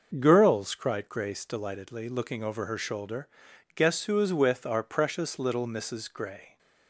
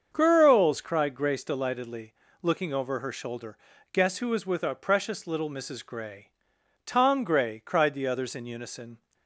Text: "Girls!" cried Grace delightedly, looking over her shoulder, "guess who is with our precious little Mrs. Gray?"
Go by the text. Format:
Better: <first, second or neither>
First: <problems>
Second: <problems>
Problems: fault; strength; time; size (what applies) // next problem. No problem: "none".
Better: first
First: none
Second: starts louder than the rest; until 1.1 s; 6.5 dB // goes on to say "Tom Gray cried the others in unison"; strong; from 6.8 s on; 2.1 s long